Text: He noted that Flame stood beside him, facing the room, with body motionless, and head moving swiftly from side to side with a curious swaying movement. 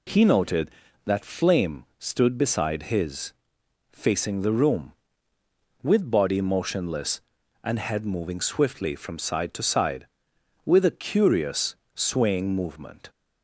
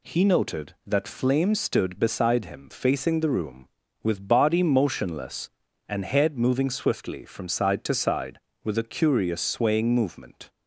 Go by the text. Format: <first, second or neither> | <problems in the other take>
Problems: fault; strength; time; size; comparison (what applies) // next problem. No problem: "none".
second | says "his" for "him"; at 2.8 s // pauses between "curious" and "swaying"; slight; at 11.7 s; 0.18 s long